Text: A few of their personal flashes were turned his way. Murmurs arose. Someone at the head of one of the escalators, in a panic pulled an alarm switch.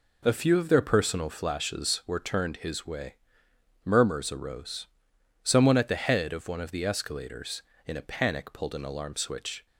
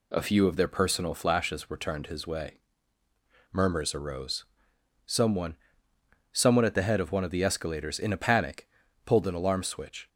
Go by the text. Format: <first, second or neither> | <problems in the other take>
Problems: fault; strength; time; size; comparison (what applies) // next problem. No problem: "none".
first | says "Someone" twice; at 6.3 s // pauses between "panic" and "pulled"; slight; at 8.6 s; 0.36 s long